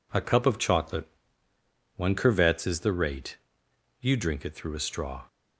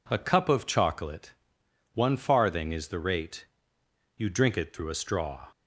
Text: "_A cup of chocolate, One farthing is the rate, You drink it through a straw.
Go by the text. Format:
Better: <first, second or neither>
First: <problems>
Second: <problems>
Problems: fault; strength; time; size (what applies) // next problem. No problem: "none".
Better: second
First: says "curvets" for "farthing"; at 2.1 s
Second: none